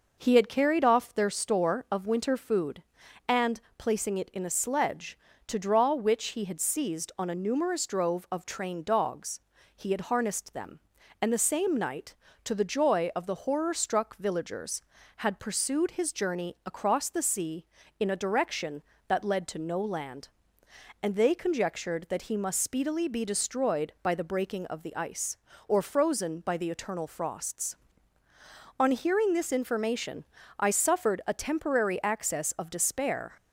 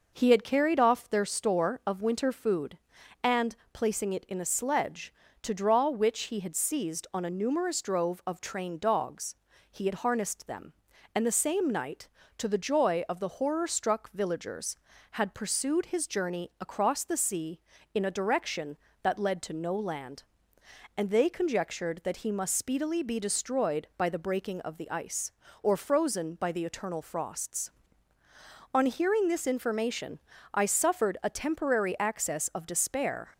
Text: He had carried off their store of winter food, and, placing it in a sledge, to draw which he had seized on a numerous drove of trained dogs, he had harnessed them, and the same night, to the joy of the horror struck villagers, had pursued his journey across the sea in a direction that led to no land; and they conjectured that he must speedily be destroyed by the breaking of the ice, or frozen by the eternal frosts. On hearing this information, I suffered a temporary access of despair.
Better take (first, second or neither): neither